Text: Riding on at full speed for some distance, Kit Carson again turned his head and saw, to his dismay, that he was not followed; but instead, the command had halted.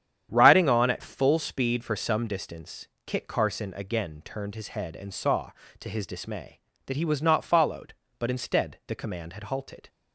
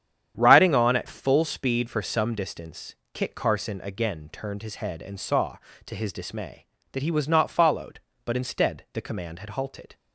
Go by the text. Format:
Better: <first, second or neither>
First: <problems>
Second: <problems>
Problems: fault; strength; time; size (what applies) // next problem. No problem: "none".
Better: neither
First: starts louder than the rest; strong; until 1.3 s; 9 dB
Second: starts louder than the rest; strong; until 1.3 s; 9 dB